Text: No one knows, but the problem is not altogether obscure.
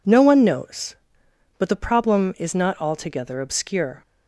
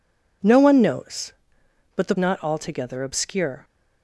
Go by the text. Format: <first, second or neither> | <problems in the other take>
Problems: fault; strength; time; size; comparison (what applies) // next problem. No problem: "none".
first | skips "problem is"; at 2.1 s